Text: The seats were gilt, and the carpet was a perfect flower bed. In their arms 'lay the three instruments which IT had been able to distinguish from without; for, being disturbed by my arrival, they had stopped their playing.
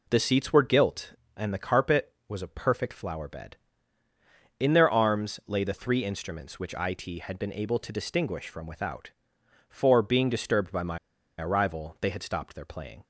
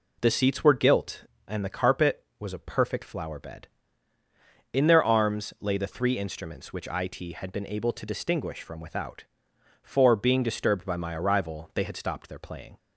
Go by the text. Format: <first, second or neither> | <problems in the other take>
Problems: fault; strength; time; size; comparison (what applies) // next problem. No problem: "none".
second | pauses between "my" and "arrival"; at 10.9 s; 0.42 s long